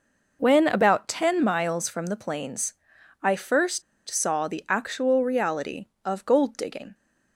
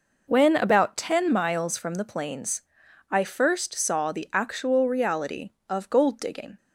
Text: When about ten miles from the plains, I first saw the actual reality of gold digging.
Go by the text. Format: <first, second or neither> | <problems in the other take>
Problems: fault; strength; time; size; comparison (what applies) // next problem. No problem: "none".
second | pauses between "first" and "saw"; slight; at 3.8 s; 0.25 s long